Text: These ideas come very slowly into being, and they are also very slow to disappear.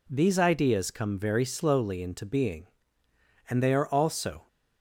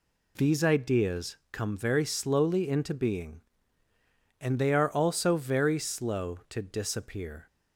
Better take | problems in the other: second | stops before "very slow to disappear"; at 4.4 s

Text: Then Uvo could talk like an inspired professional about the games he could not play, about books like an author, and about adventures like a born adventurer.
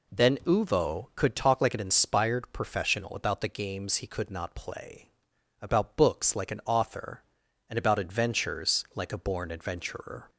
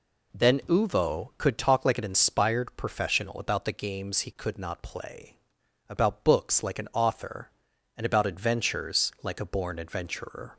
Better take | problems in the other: neither | none

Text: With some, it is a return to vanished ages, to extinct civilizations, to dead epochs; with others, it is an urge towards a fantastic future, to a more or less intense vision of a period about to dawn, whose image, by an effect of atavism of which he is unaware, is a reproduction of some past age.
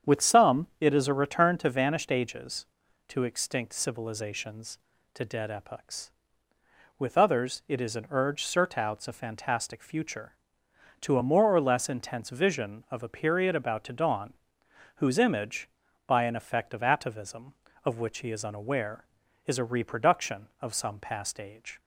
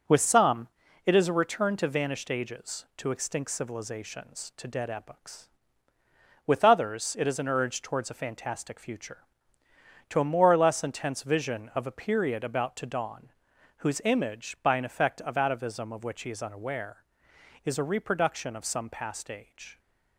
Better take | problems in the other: second | starts louder than the rest; strong; until 1.2 s; 8 dB // says "surtouts" for "towards"; at 8.4 s

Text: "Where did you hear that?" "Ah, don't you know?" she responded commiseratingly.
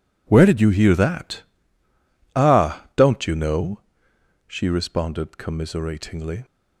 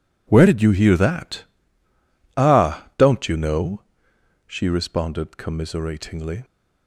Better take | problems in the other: neither | none

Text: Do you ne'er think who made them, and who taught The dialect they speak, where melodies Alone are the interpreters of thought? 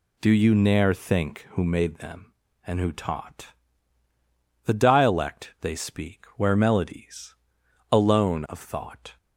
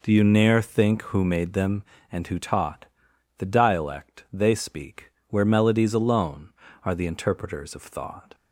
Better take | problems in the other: second | pauses between "taught" and "The"; at 3.4 s; 1.1 s long; noticeable in the second // pauses between "melodies" and "Alone"; noticeable; at 7.3 s; 0.56 s long // skips "are the interpreters"; at 8.4 s

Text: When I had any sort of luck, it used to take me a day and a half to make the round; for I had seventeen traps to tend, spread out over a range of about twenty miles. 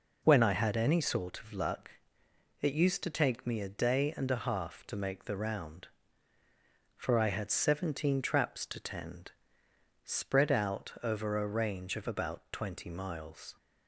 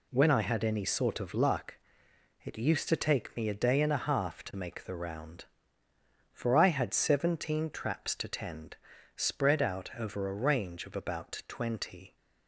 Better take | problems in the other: first | stops before "miles"; at 12.1 s

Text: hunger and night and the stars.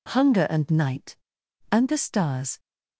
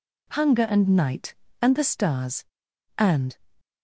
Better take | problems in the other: first | goes on to say "And"; slight; from 2.9 s on; 0.38 s long

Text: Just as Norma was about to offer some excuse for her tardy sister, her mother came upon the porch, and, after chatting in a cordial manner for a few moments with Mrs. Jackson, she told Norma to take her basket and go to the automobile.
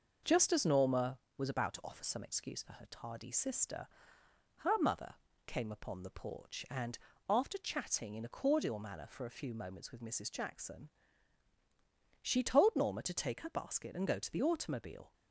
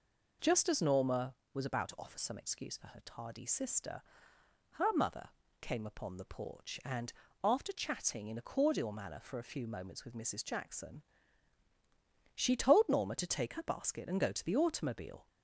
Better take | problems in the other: second | gets quieter; throughout; 3.5 dB // pauses between "mother" and "came"; slight; at 5.1 s; 0.32 s long; slight in the second

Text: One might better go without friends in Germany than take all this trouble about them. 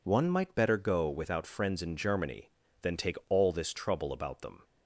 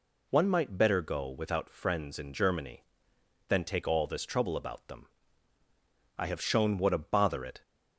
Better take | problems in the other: first | goes on to say "I have shown what a bother it"; from 6.1 s on; 1.4 s long

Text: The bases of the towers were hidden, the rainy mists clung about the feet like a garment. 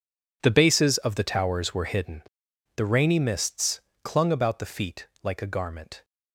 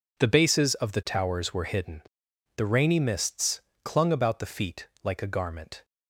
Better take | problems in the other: second | gets quieter; strong; throughout; 15.5 dB // pauses between "mists" and "clung"; slight; at 3.8 s; 0.22 s long; slight in the second // pauses between "feet" and "like"; slight; at 5.0 s; 0.16 s long; slight in the second

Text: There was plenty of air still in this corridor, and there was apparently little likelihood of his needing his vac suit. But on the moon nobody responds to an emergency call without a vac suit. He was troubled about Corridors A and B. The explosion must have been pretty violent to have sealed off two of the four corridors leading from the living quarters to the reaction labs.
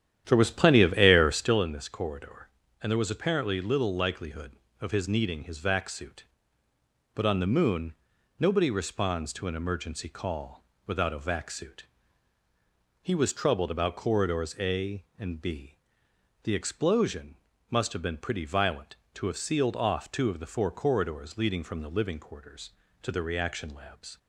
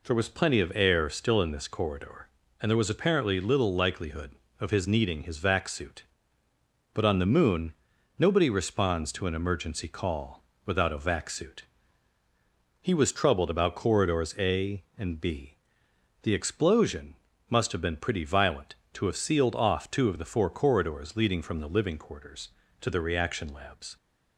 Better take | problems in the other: second | starts louder than the rest; strong; until 1.6 s; 10.5 dB // pauses between "moon" and "nobody"; at 7.9 s; 0.44 s long; also in the second // pauses between "call" and "without"; slight; at 10.6 s; 0.22 s long; slight in the second // pauses between "explosion" and "must"; slight; at 17.3 s; 0.34 s long; slight in the second

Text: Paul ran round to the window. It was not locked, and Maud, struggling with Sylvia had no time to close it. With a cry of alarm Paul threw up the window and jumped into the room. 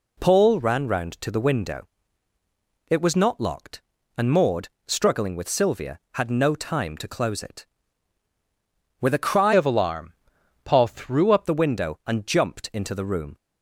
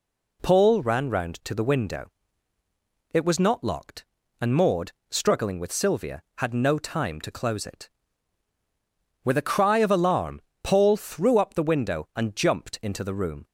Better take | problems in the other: second | changes voice from "of" to "up"; from 9.5 to 11.4 s; 1.9 s long // pauses between "alarm" and "Paul"; noticeable; at 10.1 s; 0.52 s long; slight in the second

